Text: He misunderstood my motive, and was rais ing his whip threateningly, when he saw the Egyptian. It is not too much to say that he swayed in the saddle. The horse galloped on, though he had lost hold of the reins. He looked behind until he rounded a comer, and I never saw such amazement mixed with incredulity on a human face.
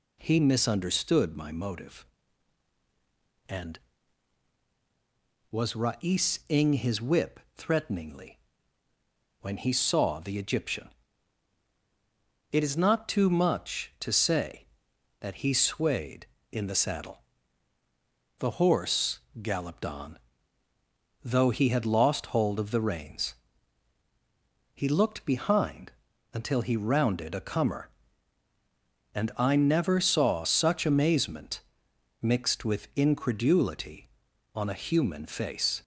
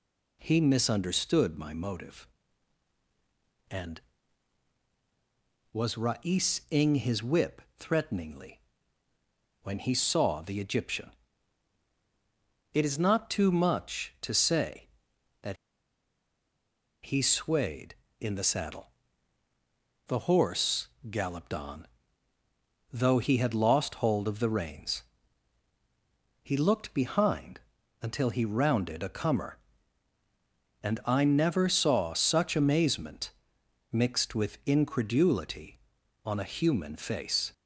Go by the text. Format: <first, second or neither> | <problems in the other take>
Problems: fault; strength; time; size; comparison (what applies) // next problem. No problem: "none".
first | pauses between "that" and "he"; strong; at 15.5 s; 1.4 s long // pauses between "horse" and "galloped"; slight; at 20.8 s; 0.20 s long; slight in the first // pauses between "behind" and "until"; at 27.6 s; 0.40 s long; also in the first // pauses between "amazement" and "mixed"; noticeable; at 33.3 s; 0.60 s long; noticeable in the first